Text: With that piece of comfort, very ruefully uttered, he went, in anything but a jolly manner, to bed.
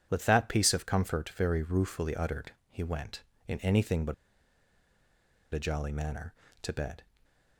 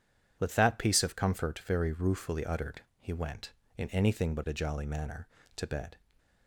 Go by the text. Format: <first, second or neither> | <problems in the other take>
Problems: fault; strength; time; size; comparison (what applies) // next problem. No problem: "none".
second | pauses between "but" and "a"; strong; at 4.1 s; 1.3 s long